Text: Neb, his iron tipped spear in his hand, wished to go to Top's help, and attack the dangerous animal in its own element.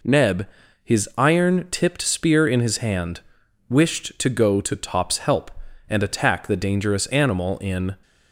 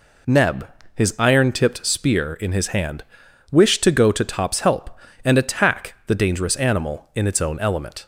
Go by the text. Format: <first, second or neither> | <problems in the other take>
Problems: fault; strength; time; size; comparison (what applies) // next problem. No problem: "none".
second | stops before "its own element"; at 8.0 s